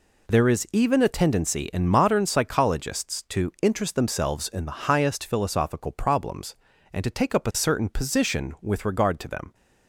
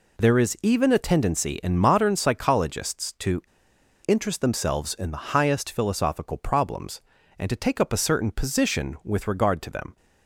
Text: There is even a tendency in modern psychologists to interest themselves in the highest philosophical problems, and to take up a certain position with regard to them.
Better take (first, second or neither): first